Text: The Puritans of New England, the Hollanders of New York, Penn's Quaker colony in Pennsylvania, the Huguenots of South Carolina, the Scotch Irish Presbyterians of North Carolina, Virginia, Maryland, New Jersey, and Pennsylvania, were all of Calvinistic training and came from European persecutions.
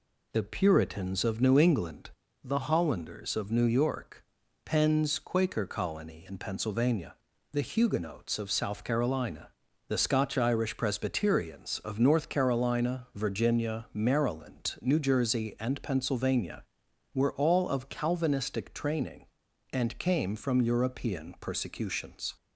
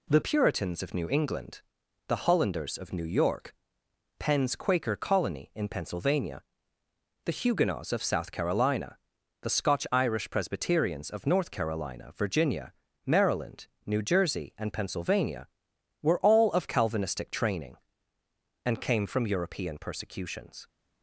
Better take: first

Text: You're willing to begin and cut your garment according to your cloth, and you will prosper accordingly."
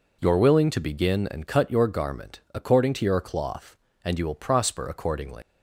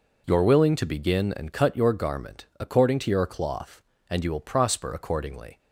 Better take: second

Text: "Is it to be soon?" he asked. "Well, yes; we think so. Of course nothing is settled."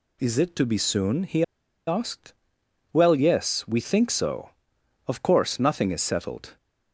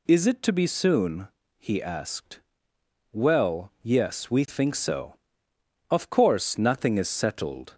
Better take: second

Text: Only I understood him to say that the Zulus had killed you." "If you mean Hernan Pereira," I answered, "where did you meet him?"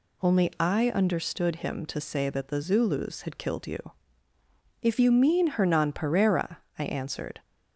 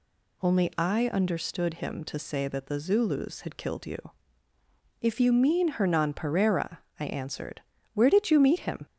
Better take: second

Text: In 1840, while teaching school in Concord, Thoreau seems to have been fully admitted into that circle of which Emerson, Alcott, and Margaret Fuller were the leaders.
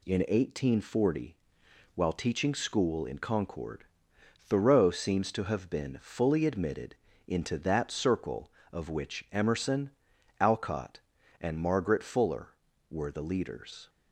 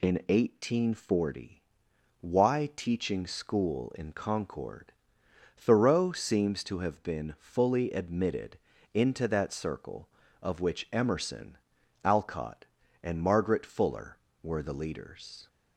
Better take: first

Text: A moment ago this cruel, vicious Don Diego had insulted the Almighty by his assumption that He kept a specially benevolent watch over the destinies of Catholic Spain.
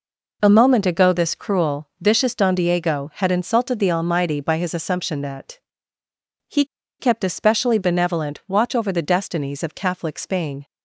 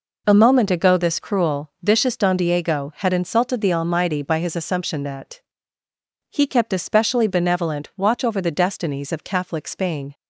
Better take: second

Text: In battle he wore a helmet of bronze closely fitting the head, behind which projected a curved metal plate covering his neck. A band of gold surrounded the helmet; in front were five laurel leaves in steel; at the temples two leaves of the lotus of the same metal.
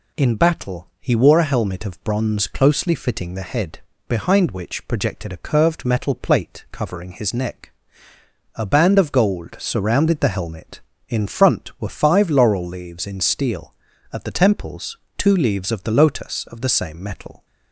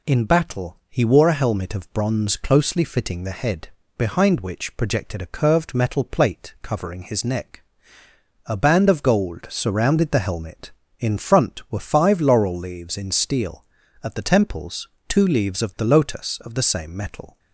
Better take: neither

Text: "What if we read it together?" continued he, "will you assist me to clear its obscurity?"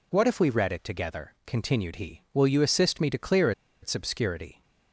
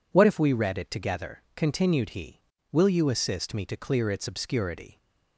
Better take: second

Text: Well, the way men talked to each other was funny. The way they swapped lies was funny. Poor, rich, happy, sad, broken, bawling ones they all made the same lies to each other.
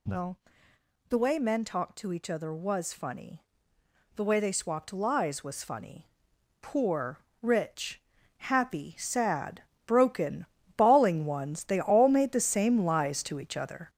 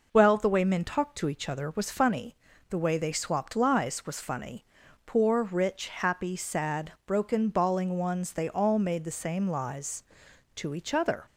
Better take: second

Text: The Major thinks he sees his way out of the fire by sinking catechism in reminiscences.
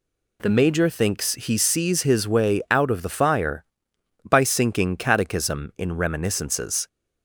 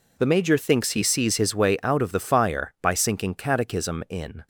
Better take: first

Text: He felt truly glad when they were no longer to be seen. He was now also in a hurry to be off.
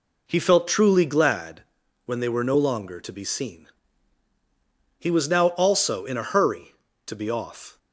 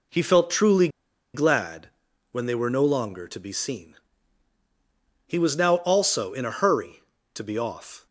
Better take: first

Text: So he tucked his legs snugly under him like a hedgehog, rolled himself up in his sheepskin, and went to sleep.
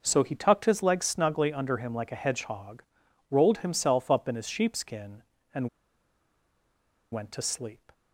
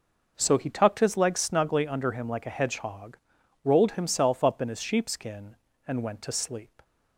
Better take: second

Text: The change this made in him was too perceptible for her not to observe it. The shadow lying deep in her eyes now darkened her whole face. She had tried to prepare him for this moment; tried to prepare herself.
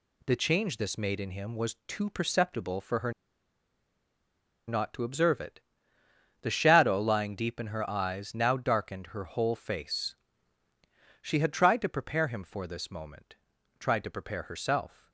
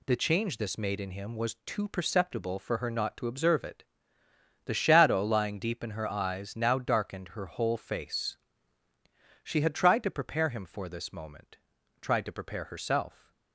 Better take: second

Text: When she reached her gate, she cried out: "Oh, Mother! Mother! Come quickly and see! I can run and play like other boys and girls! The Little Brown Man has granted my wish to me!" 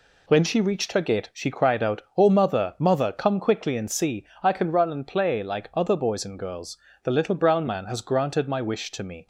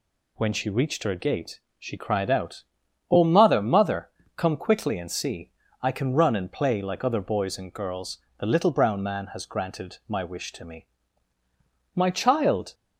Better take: first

